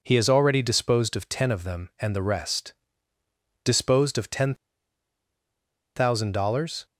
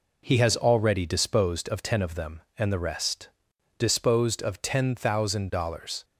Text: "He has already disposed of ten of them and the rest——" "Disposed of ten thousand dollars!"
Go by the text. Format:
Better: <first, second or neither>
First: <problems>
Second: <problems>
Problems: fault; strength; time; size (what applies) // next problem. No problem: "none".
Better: second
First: pauses between "ten" and "thousand"; strong; at 4.5 s; 1.4 s long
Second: none